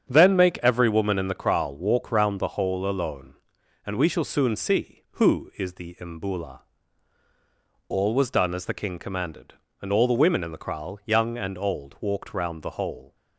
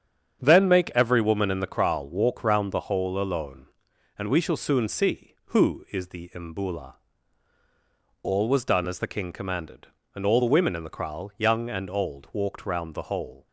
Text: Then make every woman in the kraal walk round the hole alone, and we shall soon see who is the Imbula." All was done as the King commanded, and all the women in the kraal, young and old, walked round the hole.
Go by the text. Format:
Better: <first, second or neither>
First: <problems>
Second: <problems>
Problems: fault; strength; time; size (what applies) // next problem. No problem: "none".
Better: neither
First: starts louder than the rest; strong; until 1.1 s; 7.5 dB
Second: starts louder than the rest; strong; until 1.4 s; 7.5 dB